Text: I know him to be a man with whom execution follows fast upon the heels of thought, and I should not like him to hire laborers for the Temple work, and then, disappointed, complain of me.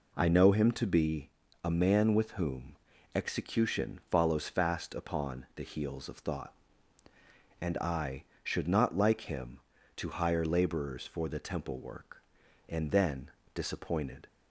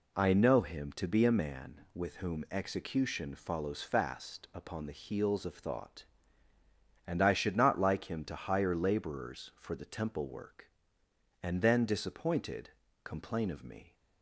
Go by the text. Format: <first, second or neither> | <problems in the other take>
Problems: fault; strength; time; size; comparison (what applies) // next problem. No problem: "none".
second | pauses between "be" and "a"; slight; at 1.2 s; 0.34 s long // pauses between "whom" and "execution"; at 2.7 s; 0.40 s long // stops before "complain of me"; at 14.2 s